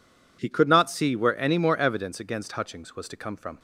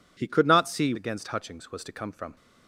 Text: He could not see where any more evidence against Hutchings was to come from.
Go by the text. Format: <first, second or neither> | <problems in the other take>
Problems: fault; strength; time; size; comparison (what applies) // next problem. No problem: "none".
first | skips "where any more evidence"; at 0.9 s